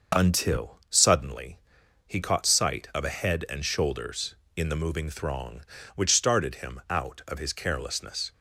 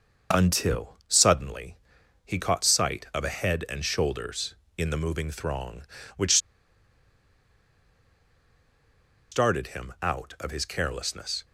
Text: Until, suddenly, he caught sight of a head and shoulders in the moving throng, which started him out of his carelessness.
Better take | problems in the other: first | starts louder than the rest; noticeable; until 1.4 s; 6 dB // pauses between "which" and "started"; strong; at 6.3 s; 2.9 s long

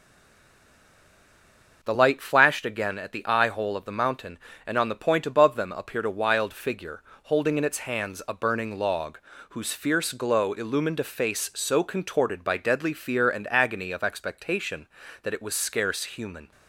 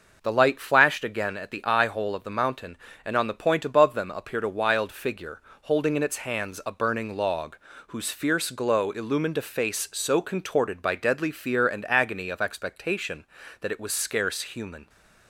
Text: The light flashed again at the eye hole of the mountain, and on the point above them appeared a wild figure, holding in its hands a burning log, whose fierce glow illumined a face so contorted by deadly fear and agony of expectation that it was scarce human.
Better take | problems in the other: second | stays silent before the first word; noticeable; until 1.8 s; 1.8 s long // starts louder than the rest; until 2.8 s; 6 dB; also in the second

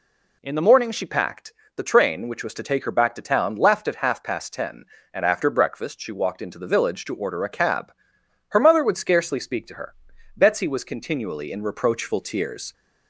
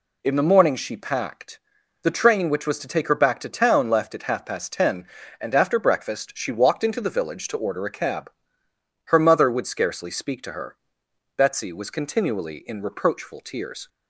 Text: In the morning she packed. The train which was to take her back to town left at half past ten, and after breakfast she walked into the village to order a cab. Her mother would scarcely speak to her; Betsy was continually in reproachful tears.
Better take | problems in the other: neither | none

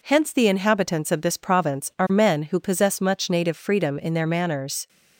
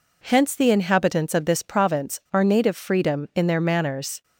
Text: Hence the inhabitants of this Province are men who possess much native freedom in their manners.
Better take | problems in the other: first | skips "men who possess much"; at 2.4 s

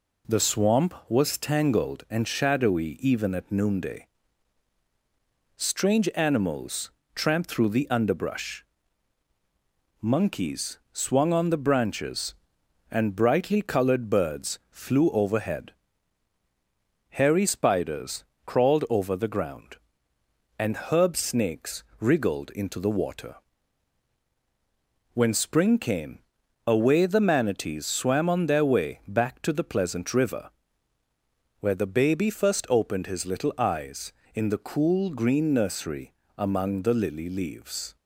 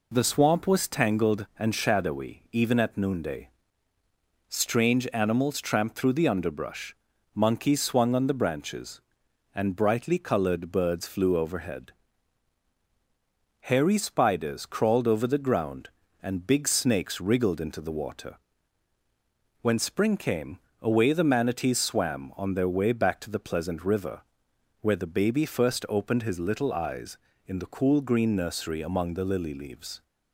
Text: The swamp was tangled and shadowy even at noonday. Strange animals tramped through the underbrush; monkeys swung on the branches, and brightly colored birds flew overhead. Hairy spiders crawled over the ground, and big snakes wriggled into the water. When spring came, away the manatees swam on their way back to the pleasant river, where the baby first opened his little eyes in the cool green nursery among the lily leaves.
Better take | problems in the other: second | pauses between "animals" and "tramped"; slight; at 6.8 s; 0.24 s long // pauses between "spiders" and "crawled"; slight; at 18.2 s; 0.22 s long // says "herb" for "big"; at 20.8 s // pauses between "snakes" and "wriggled"; slight; at 21.8 s; 0.16 s long // pauses between "nursery" and "among"; slight; at 36.1 s; 0.24 s long

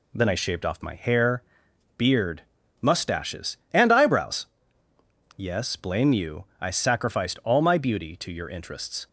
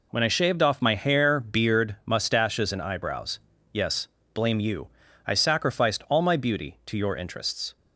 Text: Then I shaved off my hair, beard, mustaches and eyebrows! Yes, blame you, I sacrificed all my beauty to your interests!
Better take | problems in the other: first | says "When" for "Then"; at 0.1 s

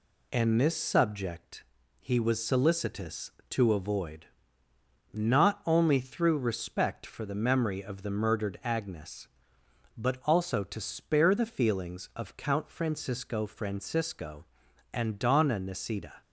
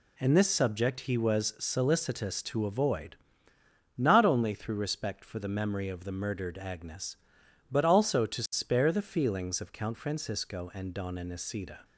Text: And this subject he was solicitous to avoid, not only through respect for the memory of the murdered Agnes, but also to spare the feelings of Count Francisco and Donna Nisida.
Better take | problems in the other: second | pauses between "subject" and "he"; at 1.6 s; 0.38 s long // says "Francisco" twice; at 13.4 s

